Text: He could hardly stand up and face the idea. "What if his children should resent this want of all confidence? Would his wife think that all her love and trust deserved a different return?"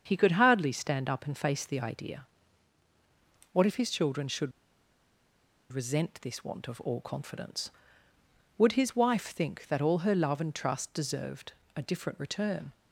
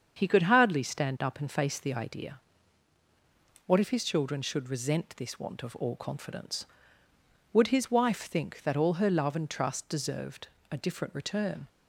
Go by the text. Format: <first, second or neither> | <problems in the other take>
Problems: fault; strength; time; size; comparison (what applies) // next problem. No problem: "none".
second | starts louder than the rest; strong; until 1.0 s; 7 dB; strong in the second // pauses between "should" and "resent"; at 4.5 s; 1.2 s long // pauses between "deserved" and "a"; slight; at 11.5 s; 0.22 s long; slight in the second